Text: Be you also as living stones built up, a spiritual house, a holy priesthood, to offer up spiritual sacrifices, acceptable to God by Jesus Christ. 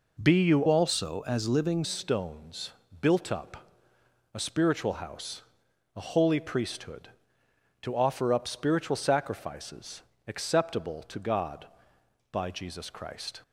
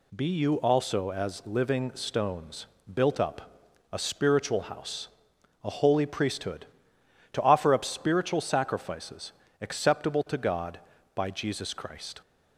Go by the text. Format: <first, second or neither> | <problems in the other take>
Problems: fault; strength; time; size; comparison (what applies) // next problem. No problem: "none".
second | changes voice from "also" to "living"; from 0.6 to 1.8 s; 1.2 s long // pauses between "stones" and "built"; slight; at 2.7 s; 0.28 s long; slight in the second